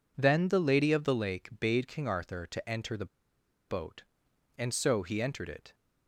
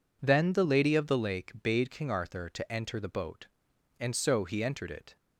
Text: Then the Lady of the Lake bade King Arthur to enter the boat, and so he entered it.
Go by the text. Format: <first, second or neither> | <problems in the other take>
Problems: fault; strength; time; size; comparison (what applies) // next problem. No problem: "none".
second | pauses between "the" and "boat"; noticeable; at 3.0 s; 0.61 s long